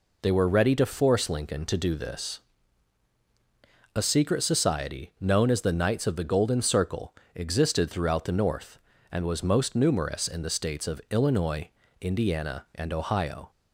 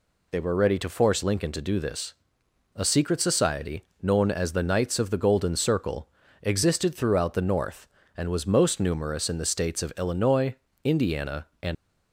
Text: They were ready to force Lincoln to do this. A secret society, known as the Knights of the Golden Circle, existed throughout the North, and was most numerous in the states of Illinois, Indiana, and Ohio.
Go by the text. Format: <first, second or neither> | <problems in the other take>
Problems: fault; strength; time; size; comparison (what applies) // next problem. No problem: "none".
first | stops before "Ohio"; at 11.7 s